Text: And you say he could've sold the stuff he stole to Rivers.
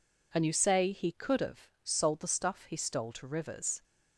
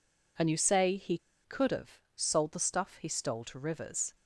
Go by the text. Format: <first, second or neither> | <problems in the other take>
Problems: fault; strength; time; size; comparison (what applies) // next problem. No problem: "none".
first | pauses between "he" and "could've"; slight; at 1.1 s; 0.27 s long // pauses between "could've" and "sold"; slight; at 1.9 s; 0.16 s long